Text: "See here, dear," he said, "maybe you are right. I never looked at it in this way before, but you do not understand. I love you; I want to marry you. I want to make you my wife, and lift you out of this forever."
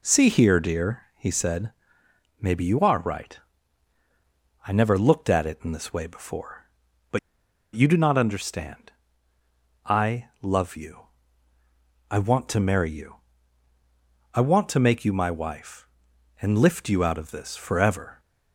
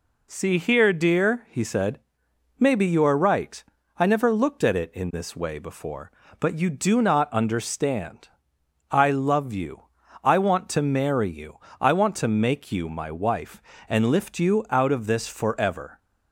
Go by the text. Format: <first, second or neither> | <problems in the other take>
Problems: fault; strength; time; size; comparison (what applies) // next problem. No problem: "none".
second | pauses between "but" and "you"; noticeable; at 7.1 s; 0.56 s long